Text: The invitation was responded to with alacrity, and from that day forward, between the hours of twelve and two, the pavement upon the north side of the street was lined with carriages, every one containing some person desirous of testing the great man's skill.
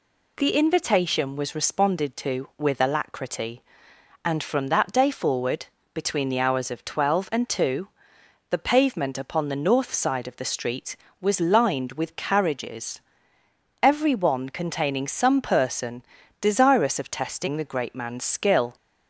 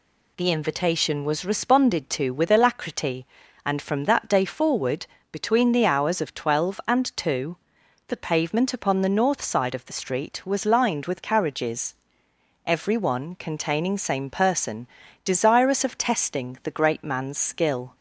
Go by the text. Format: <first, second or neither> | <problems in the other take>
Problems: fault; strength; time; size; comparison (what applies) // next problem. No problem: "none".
first | says "same" for "some"; at 13.9 s // pauses between "person" and "desirous"; slight; at 14.8 s; 0.36 s long; also in the first